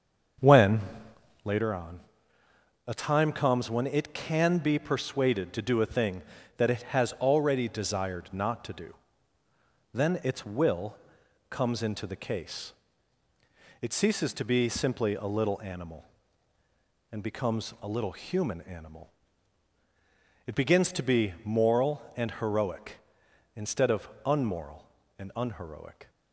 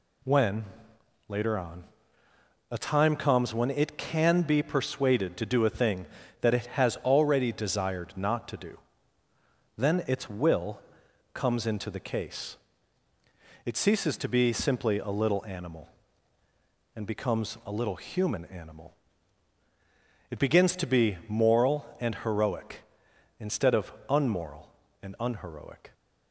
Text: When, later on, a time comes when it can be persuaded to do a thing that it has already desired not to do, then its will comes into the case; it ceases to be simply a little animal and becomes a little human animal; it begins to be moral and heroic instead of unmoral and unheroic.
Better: second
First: starts louder than the rest; until 1.7 s; 7 dB // pauses between "will" and "comes"; noticeable; at 10.9 s; 0.54 s long // pauses between "of" and "unmoral"; slight; at 24.0 s; 0.16 s long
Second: pauses between "will" and "comes"; noticeable; at 10.7 s; 0.54 s long // pauses between "of" and "unmoral"; slight; at 23.9 s; 0.16 s long

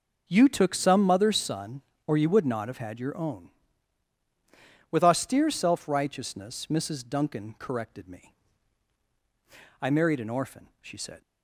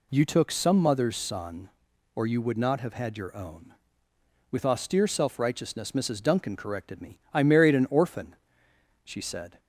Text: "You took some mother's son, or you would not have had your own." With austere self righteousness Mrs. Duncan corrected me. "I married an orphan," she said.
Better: neither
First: none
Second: none

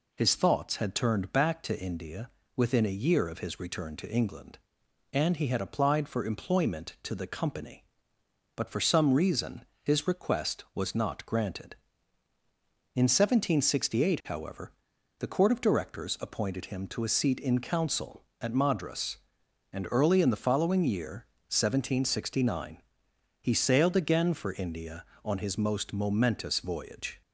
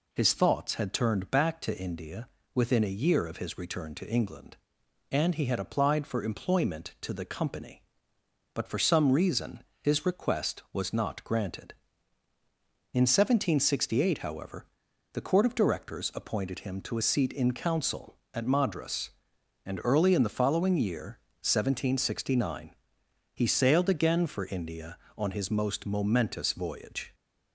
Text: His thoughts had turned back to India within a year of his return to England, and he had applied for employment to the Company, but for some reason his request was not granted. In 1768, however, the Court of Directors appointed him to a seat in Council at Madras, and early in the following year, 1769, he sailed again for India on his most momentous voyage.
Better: neither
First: pauses between "India" and "within"; slight; at 2.2 s; 0.26 s long // pauses between "reason" and "his"; slight; at 9.6 s; 0.18 s long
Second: pauses between "India" and "within"; slight; at 2.2 s; 0.26 s long // pauses between "reason" and "his"; slight; at 9.6 s; 0.18 s long

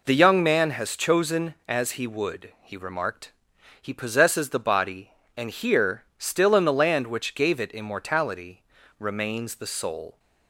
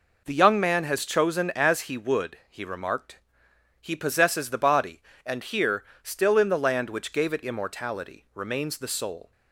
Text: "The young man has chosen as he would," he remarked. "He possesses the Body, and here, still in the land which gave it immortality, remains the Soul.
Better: neither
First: none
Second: none

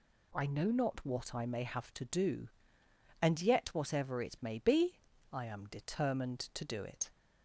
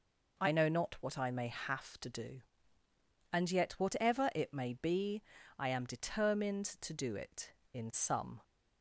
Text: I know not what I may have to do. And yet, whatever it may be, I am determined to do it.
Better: first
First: none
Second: goes on to say "In some"; noticeable; from 7.7 s on; 0.68 s long

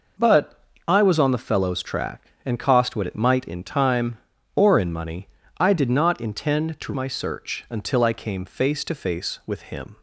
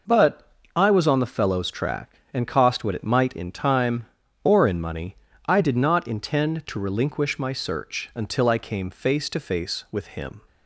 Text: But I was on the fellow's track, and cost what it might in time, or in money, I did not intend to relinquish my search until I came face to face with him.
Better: second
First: pauses between "But" and "I"; slight; at 0.5 s; 0.28 s long // skips "relinquish"; at 6.9 s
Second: pauses between "But" and "I"; slight; at 0.4 s; 0.28 s long

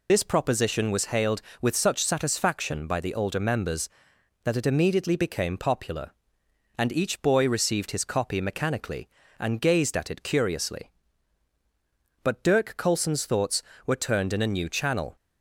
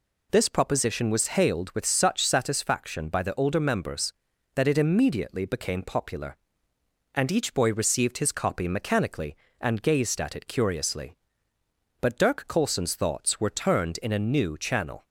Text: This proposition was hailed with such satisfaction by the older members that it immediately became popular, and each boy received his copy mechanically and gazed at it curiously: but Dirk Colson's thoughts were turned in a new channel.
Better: second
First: loses the start of "This"; at 0.0 s; 55 ms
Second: none

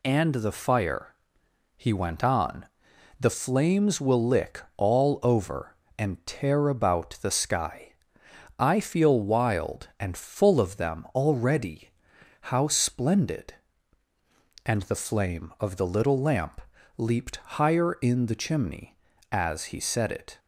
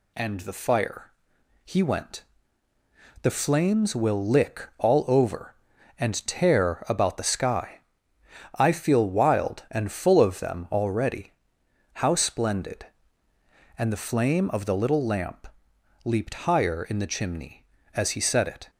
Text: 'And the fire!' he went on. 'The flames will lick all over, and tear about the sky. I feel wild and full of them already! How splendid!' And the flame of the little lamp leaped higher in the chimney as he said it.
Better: first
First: pauses between "lamp" and "leaped"; slight; at 16.6 s; 0.34 s long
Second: skips "on"; at 2.7 s // pauses between "lamp" and "leaped"; noticeable; at 15.4 s; 0.56 s long

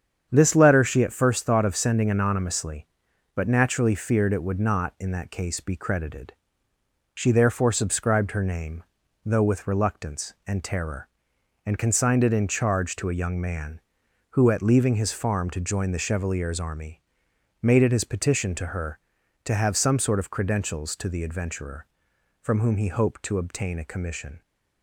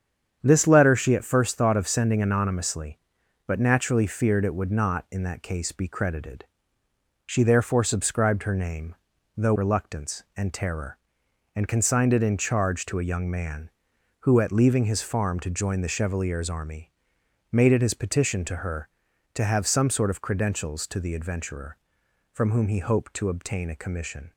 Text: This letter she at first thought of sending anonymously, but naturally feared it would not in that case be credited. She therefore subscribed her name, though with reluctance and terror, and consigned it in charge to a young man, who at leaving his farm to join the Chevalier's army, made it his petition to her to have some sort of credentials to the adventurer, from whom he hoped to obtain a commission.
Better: first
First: starts louder than the rest; strong; until 1.3 s; 8 dB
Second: starts louder than the rest; strong; until 1.4 s; 8 dB // skips "with"; at 9.5 s

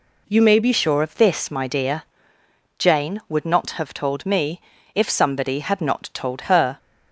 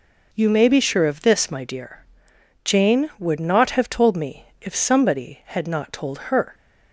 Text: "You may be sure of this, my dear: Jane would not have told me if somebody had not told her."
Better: second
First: changes voice at "sure"; from 0.7 s on; 6.0 s long // pauses between "me" and "if"; slight; at 4.6 s; 0.34 s long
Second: pauses between "me" and "if"; slight; at 4.4 s; 0.16 s long

